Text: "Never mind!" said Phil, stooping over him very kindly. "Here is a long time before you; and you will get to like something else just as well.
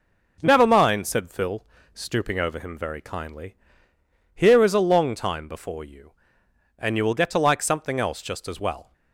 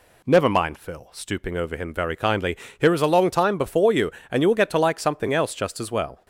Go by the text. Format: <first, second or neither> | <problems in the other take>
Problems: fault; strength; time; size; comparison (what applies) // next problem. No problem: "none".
first | skips "said"; at 0.7 s